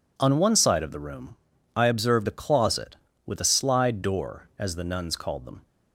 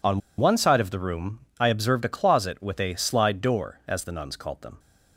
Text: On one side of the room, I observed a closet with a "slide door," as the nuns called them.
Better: first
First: none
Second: pauses between "On" and "one"; slight; at 0.2 s; 0.18 s long

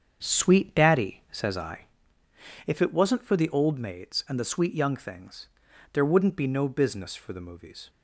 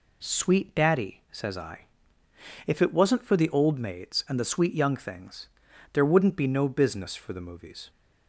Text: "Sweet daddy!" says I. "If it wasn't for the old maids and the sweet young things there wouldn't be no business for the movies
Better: second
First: starts louder than the rest; strong; until 2.0 s; 7 dB // pauses between "things" and "there"; noticeable; at 5.4 s; 0.46 s long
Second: pauses between "things" and "there"; noticeable; at 5.4 s; 0.46 s long

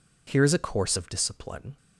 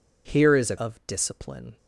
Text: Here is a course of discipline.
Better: first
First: none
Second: skips "course"; at 0.7 s

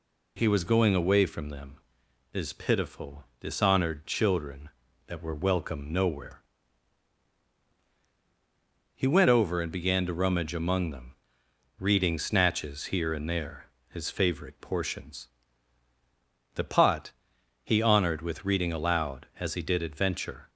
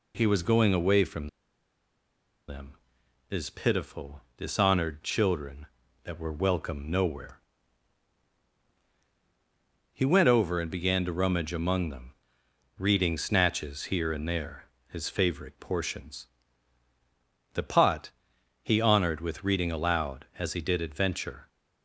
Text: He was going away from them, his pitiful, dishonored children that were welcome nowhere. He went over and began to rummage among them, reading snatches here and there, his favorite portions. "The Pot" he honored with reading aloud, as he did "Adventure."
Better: first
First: pauses between "Pot" and "he"; noticeable; at 17.1 s; 0.52 s long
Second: pauses between "from" and "them"; at 1.2 s; 1.2 s long // pauses between "Pot" and "he"; noticeable; at 18.1 s; 0.52 s long

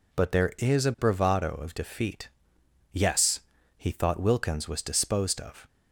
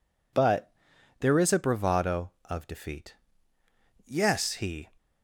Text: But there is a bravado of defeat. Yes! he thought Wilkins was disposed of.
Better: first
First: none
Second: pauses between "But" and "there"; noticeable; at 0.7 s; 0.48 s long // stops before "thought Wilkins was disposed of"; at 4.9 s

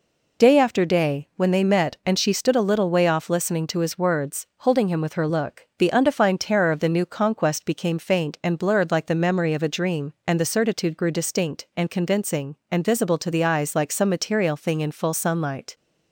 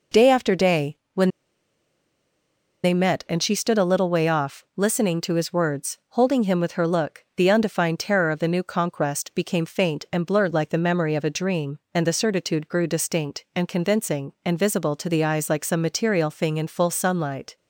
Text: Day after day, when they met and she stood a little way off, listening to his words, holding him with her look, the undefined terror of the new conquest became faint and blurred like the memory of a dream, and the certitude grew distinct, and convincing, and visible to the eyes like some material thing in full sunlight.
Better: first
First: none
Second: pauses between "when" and "they"; strong; at 1.3 s; 1.5 s long

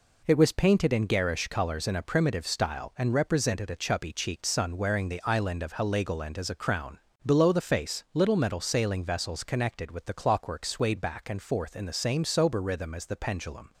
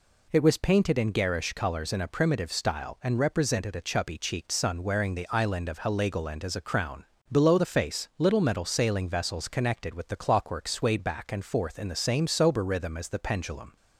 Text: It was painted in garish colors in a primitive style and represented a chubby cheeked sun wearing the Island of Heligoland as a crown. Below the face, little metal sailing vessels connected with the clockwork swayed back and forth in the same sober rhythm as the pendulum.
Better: second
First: gets quieter; noticeable; throughout; 6 dB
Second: none

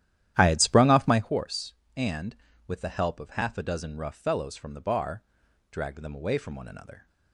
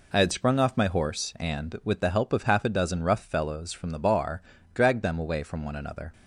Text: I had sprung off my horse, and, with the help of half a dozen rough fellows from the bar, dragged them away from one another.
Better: second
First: starts louder than the rest; strong; until 1.3 s; 12 dB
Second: none

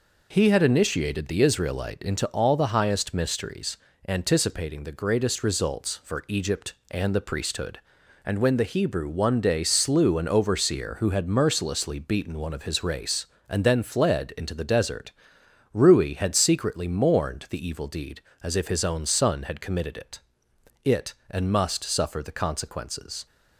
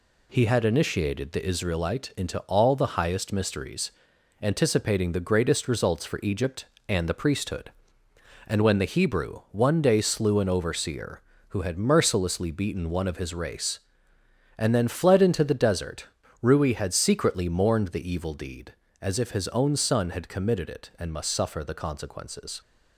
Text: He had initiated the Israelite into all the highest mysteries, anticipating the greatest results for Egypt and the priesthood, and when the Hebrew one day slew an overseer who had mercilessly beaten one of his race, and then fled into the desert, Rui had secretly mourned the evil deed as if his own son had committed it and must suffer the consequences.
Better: second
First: says "it" twice; at 20.8 s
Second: none

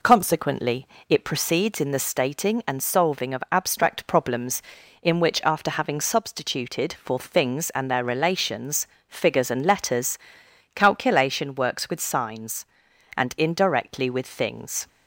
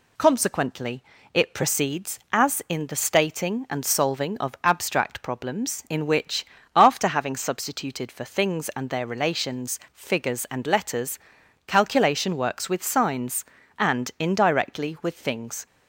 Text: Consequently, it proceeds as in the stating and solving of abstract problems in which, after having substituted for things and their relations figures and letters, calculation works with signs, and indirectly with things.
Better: second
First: skips "as"; at 1.7 s // pauses between "relations" and "figures"; slight; at 8.8 s; 0.20 s long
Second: none

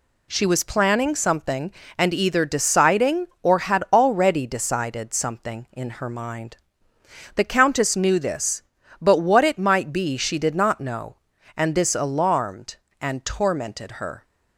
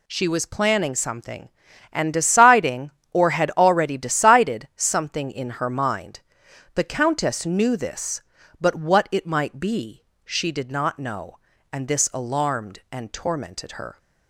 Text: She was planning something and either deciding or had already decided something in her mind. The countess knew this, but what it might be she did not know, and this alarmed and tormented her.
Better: first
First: none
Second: skips "either"; at 2.1 s // pauses between "be" and "she"; slight; at 10.0 s; 0.22 s long

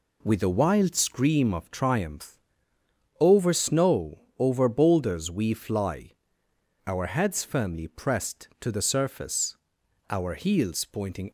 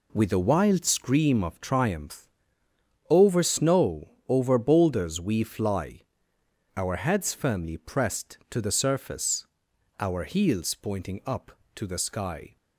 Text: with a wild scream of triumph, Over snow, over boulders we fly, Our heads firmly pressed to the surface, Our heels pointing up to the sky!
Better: second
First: stops before "up to the sky"; at 11.2 s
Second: none

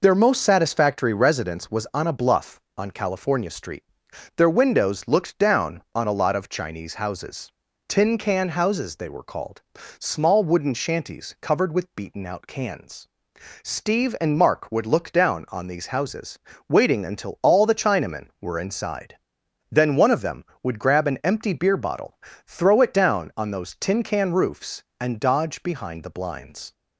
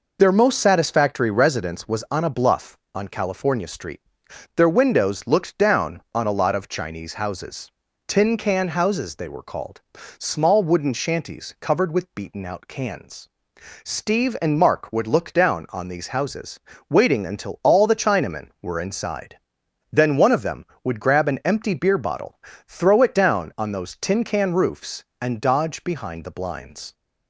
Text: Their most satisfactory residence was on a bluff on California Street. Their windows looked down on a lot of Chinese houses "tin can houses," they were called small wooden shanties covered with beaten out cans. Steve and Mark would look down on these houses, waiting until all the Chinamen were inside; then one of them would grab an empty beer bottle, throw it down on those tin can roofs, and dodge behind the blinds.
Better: neither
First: pauses between "houses" and "tin"; at 7.5 s; 0.38 s long // pauses between "called" and "small"; slight; at 9.6 s; 0.36 s long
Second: pauses between "houses" and "tin"; at 7.6 s; 0.38 s long // pauses between "called" and "small"; slight; at 9.8 s; 0.36 s long

